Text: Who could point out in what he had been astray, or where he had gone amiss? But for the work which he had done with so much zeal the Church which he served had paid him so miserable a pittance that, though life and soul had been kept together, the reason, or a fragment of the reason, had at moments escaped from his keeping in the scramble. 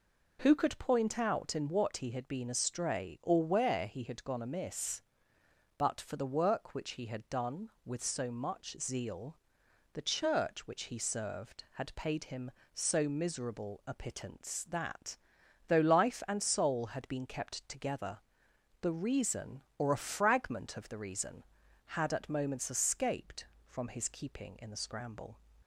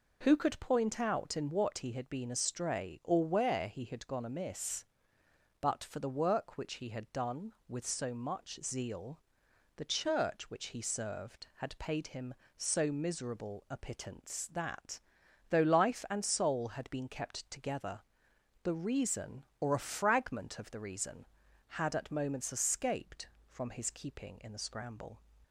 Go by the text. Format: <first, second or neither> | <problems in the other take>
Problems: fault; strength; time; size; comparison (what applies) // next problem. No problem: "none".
neither | pauses between "zeal" and "the"; noticeable; the same in both